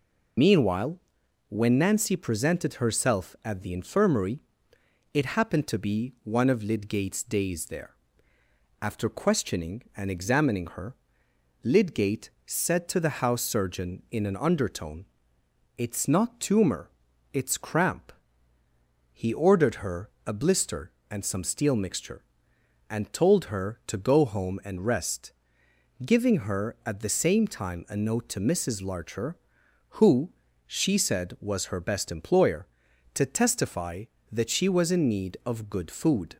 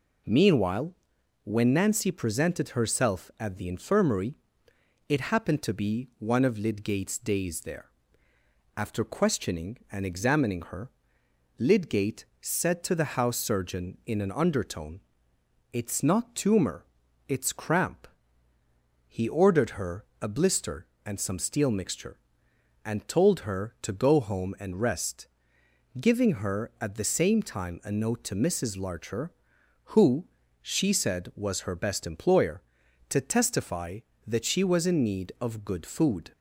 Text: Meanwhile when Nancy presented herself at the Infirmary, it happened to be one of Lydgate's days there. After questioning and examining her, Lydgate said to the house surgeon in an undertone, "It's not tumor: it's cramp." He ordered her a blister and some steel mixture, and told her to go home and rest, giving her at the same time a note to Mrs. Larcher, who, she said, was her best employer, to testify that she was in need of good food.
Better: second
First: loses the start of "Meanwhile"; at 0.3 s; 65 ms // pauses between "Meanwhile" and "when"; noticeable; at 0.9 s; 0.50 s long // pauses between "her" and "a"; slight; at 20.0 s; 0.16 s long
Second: pauses between "Meanwhile" and "when"; noticeable; at 0.9 s; 0.50 s long // pauses between "her" and "a"; slight; at 20.0 s; 0.16 s long

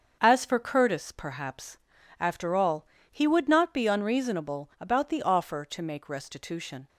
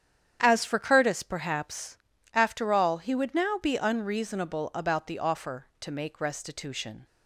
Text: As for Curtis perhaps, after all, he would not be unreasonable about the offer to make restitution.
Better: first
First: starts louder than the rest; until 1.2 s; 6.5 dB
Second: starts louder than the rest; strong; until 1.4 s; 9 dB // says "now" for "not"; at 3.3 s

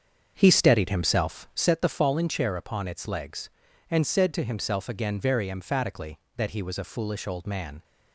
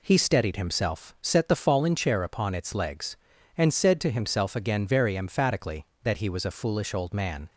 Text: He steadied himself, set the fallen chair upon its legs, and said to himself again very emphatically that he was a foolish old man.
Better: second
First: starts louder than the rest; strong; until 1.7 s; 7 dB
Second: none

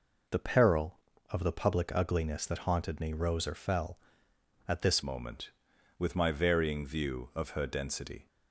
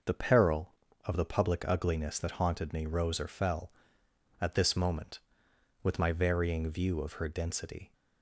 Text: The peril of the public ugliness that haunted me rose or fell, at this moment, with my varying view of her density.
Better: second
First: changes voice at "moment"; from 5.0 s on; 3.2 s long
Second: none

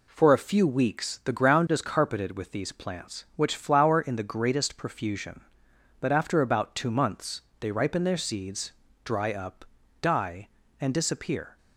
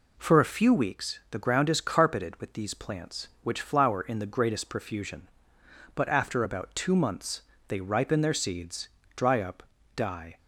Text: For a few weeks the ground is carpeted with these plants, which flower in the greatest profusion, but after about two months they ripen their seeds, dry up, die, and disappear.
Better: first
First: pauses between "months" and "they"; slight; at 7.4 s; 0.20 s long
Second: pauses between "months" and "they"; slight; at 7.4 s; 0.26 s long // stops before "and disappear"; at 10.3 s

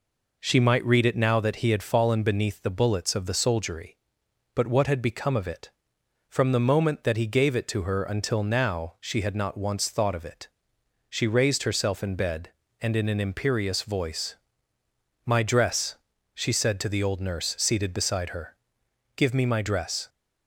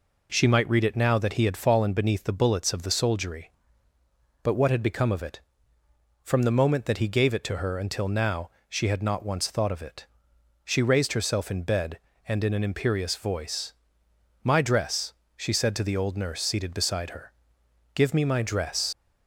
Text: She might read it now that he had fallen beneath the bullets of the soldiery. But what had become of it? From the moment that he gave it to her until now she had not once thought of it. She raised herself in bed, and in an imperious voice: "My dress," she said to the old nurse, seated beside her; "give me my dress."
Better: first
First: none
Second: pauses between "now" and "she"; slight; at 8.4 s; 0.20 s long // leaves "dress" unfinished; at 18.9 s; 80 ms

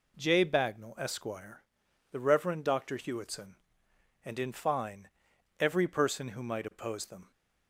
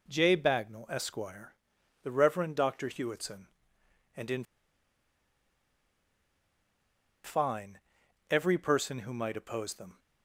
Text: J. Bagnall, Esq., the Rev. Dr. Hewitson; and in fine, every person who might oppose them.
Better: first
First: none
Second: pauses between "in" and "fine"; strong; at 4.4 s; 2.8 s long

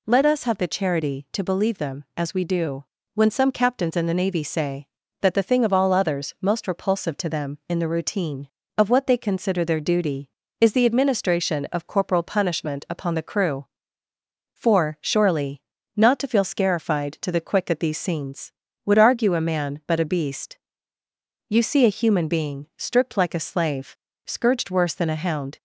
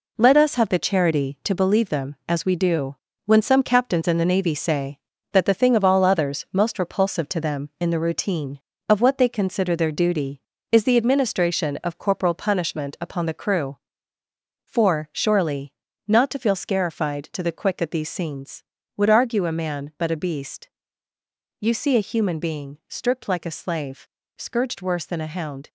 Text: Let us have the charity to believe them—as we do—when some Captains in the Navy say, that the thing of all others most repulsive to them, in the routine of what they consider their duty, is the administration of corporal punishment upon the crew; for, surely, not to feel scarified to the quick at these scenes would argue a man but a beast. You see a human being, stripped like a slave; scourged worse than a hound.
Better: first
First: none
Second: gets quieter; strong; throughout; 8.5 dB

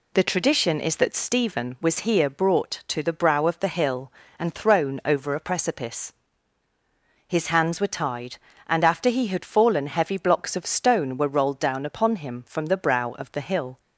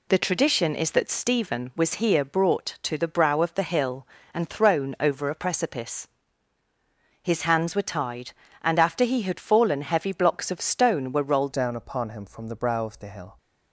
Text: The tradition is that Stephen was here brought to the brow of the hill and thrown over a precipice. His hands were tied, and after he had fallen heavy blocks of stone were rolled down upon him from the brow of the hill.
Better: first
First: none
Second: changes voice at "down"; from 11.5 s on; 1.8 s long

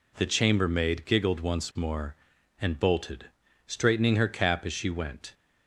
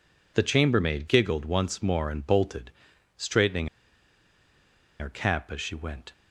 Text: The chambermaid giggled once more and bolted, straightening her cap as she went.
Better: first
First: none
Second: pauses between "straightening" and "her"; strong; at 3.6 s; 1.3 s long

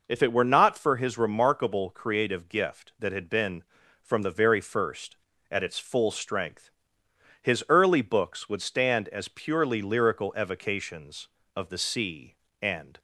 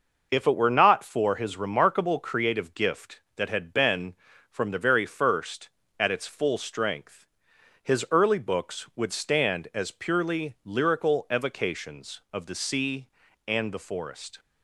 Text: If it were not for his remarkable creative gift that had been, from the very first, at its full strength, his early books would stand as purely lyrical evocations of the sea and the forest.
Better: second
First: stops before "the forest"; at 12.9 s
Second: none

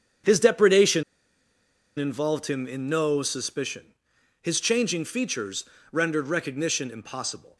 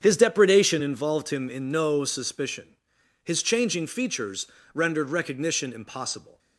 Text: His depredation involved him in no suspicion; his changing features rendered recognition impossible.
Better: second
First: starts louder than the rest; strong; until 2.2 s; 8 dB // pauses between "depredation" and "involved"; noticeable; at 1.0 s; 0.94 s long // pauses between "features" and "rendered"; slight; at 5.6 s; 0.26 s long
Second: starts louder than the rest; strong; until 1.0 s; 8 dB // pauses between "features" and "rendered"; slight; at 4.4 s; 0.26 s long

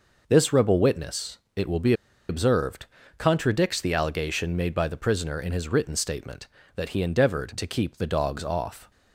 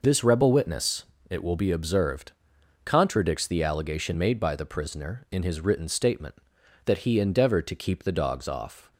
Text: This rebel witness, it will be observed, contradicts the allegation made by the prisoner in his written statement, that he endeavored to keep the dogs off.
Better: second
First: pauses between "be" and "observed"; at 1.9 s; 0.36 s long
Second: none

